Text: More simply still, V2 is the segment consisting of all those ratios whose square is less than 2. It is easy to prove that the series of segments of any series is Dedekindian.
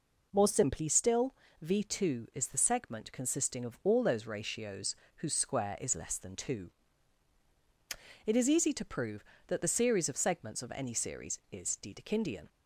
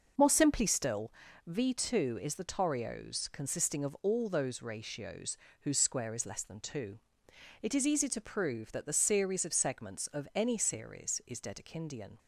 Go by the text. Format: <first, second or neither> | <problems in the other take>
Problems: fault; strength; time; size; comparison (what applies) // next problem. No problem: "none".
first | starts louder than the rest; noticeable; until 1.5 s; 6 dB // says "torios" for "segment"; at 2.4 s // pauses between "ratios" and "whose"; slight; at 5.3 s; 0.26 s long; slight in the first